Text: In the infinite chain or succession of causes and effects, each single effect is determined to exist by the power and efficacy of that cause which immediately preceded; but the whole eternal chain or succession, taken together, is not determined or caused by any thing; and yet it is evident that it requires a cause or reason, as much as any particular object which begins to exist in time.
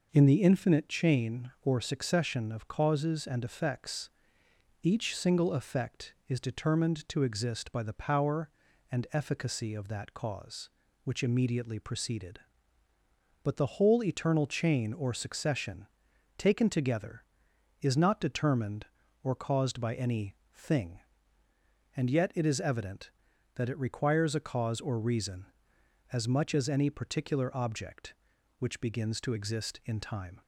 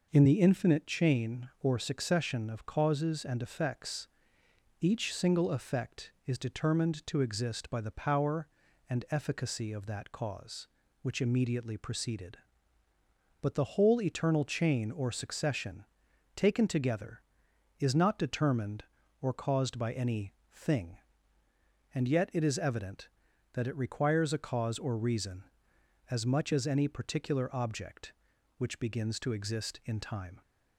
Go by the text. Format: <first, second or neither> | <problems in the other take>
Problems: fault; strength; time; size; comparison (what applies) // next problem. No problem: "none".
neither | pauses between "any" and "thing"; slight; the same in both